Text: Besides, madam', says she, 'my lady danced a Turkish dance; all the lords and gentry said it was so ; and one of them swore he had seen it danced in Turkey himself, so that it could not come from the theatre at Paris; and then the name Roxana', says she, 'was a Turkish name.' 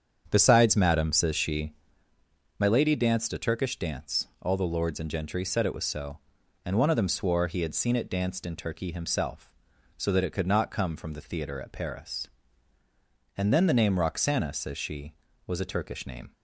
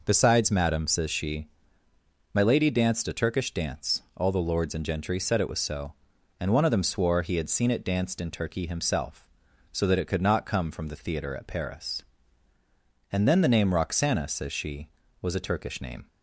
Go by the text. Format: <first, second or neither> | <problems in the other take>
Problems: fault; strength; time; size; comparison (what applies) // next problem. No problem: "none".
second | starts louder than the rest; strong; until 1.9 s; 8 dB